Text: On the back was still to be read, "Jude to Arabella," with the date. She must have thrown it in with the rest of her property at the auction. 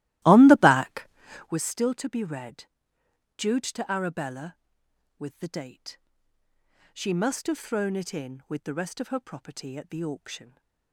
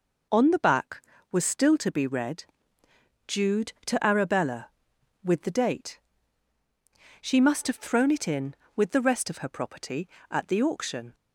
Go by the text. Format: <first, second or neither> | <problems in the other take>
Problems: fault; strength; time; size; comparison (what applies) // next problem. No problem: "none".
second | starts louder than the rest; strong; until 1.6 s; 16 dB